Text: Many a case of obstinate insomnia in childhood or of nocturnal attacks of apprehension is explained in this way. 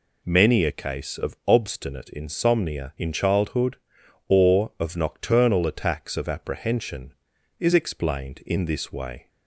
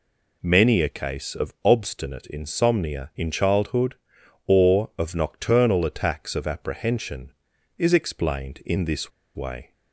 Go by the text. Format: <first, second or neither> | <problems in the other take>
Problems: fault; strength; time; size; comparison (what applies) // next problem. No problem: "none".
first | pauses between "this" and "way"; slight; at 9.1 s; 0.24 s long